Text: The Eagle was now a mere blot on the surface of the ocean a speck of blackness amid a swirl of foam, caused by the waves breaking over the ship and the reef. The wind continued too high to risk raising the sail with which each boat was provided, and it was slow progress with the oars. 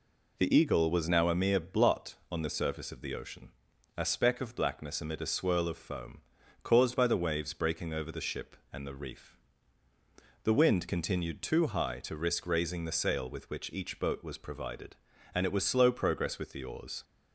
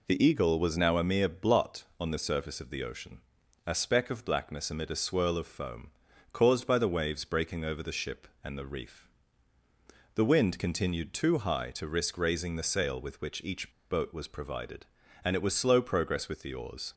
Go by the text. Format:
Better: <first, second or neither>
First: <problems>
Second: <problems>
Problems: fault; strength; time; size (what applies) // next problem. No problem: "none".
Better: first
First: pauses between "ocean" and "a"; noticeable; at 3.4 s; 0.46 s long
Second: pauses between "ocean" and "a"; noticeable; at 3.1 s; 0.46 s long // pauses between "each" and "boat"; slight; at 13.7 s; 0.20 s long